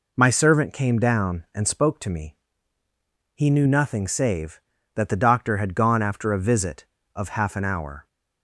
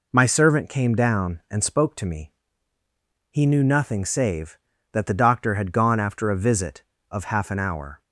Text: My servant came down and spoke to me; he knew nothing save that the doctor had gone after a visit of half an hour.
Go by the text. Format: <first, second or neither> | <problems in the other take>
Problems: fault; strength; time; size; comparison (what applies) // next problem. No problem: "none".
neither | none